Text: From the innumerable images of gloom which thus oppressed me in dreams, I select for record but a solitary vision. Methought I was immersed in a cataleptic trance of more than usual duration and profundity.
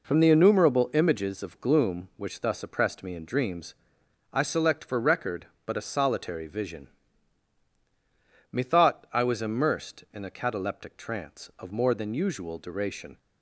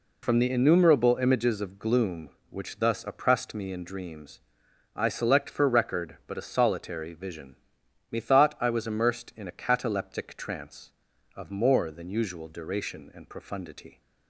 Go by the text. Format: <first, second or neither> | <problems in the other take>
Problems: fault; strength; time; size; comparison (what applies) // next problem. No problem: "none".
second | stops before "and profundity"; at 13.1 s